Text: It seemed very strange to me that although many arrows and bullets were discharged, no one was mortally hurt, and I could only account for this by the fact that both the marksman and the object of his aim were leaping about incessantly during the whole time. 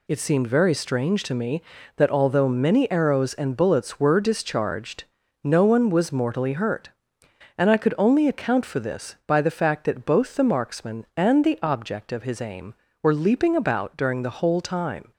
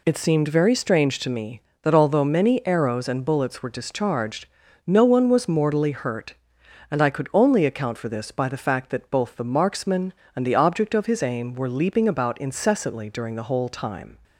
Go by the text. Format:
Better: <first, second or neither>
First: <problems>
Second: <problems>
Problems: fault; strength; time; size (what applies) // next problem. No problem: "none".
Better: second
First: skips "incessantly"; at 13.9 s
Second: none